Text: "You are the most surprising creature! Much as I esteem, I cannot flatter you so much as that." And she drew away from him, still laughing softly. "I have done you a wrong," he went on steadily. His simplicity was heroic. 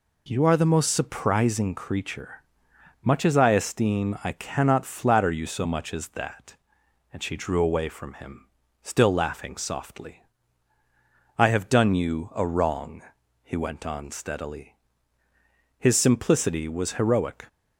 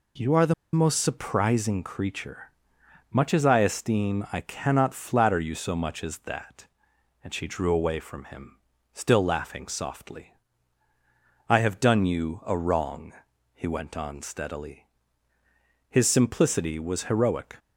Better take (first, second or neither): first